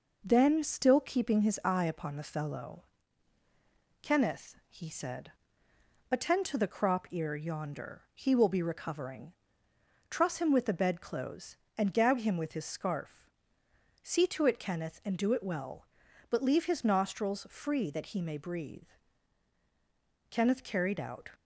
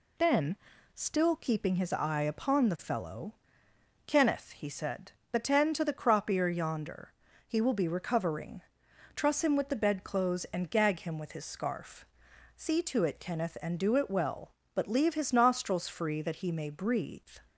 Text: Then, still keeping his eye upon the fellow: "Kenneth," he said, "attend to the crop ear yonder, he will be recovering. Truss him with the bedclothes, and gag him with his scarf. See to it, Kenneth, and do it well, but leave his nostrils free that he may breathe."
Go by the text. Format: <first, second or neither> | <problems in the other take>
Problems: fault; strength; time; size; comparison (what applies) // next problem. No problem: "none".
second | goes on to say "Kenneth carried out"; noticeable; from 20.2 s on; 1.0 s long